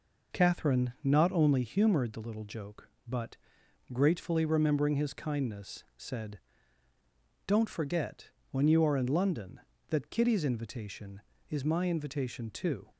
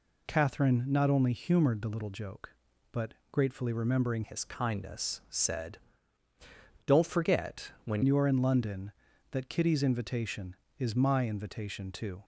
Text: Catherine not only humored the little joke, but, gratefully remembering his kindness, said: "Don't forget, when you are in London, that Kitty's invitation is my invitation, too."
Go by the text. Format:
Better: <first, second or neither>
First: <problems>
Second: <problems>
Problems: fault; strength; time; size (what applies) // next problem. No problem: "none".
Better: first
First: none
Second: changes voice from "his" to "when"; from 4.2 to 8.0 s; 3.8 s long